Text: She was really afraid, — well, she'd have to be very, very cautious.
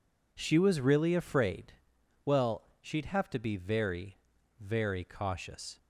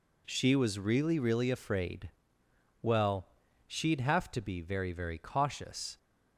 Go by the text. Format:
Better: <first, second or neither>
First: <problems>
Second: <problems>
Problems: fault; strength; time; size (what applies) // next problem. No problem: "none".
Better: first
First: none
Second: says "really" twice; at 1.1 s